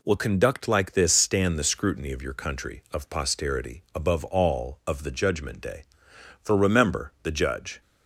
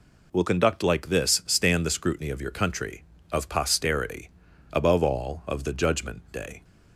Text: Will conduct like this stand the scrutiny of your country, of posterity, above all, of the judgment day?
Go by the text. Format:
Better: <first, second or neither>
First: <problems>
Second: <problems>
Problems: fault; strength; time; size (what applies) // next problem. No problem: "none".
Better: second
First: goes on to say "For remember the Judge"; from 6.4 s on; 1.3 s long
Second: none